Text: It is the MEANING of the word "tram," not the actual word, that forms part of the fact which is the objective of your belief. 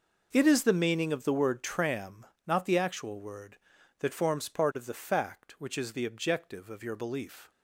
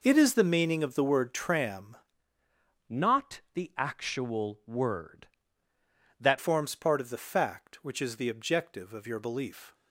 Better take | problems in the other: first | changes voice from "not" to "that"; from 2.8 to 6.3 s; 3.5 s long

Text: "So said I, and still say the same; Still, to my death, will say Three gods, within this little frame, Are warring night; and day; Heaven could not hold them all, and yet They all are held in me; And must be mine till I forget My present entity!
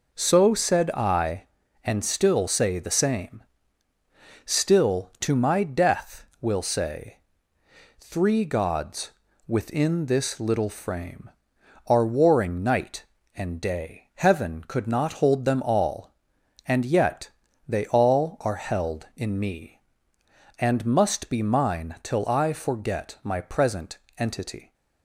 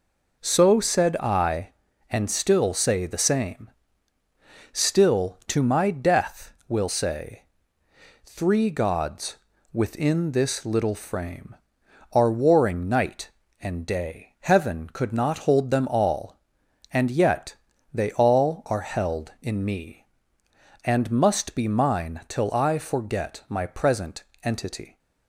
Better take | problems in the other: neither | pauses between "say" and "Three"; noticeable; the same in both // pauses between "yet" and "They"; the same in both // pauses between "present" and "entity"; slight; the same in both

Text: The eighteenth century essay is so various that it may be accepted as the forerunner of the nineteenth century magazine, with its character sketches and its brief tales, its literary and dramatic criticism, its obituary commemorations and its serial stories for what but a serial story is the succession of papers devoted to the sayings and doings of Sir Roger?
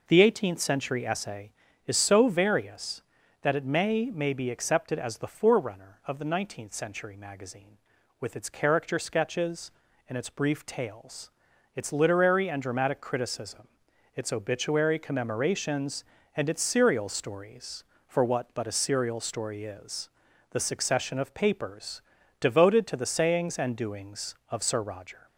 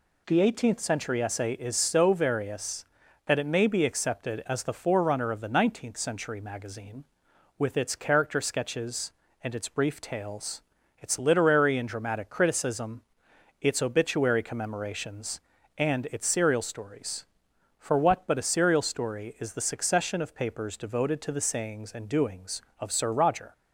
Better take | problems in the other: second | says "may" twice; at 4.1 s // pauses between "is" and "the"; at 20.0 s; 0.42 s long // pauses between "papers" and "devoted"; at 21.9 s; 0.40 s long

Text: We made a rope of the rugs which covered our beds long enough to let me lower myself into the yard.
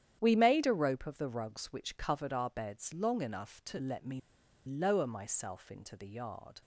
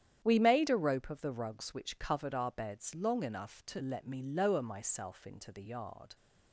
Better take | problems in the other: second | starts louder than the rest; strong; until 1.2 s; 10 dB; strong in the second // pauses between "me" and "lower"; noticeable; at 4.1 s; 0.46 s long

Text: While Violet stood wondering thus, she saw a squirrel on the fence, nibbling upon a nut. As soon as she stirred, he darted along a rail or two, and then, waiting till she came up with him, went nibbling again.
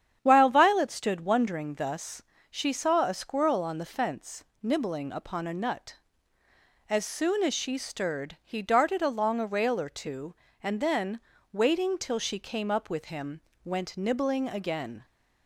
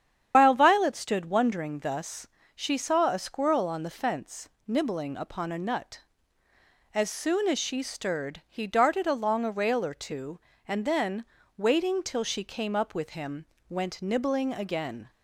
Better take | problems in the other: first | loses the start of "While"; at 0.3 s; 90 ms // starts louder than the rest; strong; until 1.3 s; 9 dB; strong in the first

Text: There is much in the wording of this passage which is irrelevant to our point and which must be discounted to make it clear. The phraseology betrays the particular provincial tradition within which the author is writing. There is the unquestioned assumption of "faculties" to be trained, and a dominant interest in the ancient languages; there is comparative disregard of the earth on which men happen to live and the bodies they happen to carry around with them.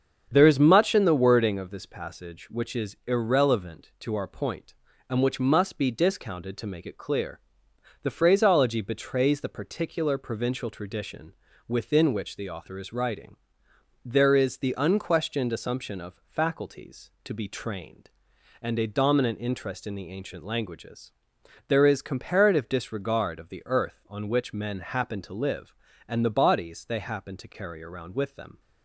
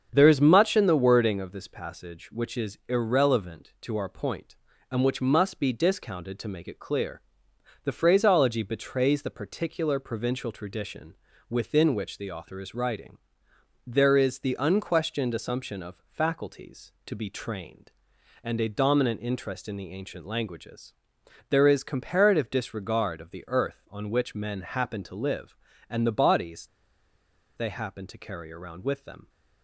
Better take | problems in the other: first | starts louder than the rest; strong; until 1.1 s; 7 dB; strong in the first // pauses between "tradition" and "within"; slight; at 11.1 s; 0.34 s long; slight in the first // pauses between "bodies" and "they"; noticeable; at 26.6 s; 0.90 s long

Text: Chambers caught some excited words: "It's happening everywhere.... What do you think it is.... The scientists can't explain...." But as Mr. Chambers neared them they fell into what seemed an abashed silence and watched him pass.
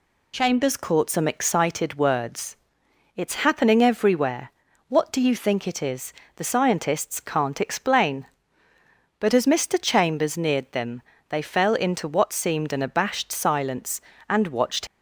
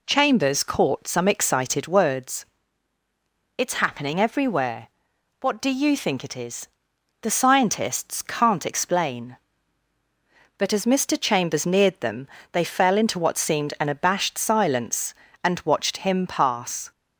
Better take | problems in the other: second | pauses between "them" and "they"; slight; at 11.0 s; 0.26 s long; slight in the second // stops before "him pass"; at 14.8 s

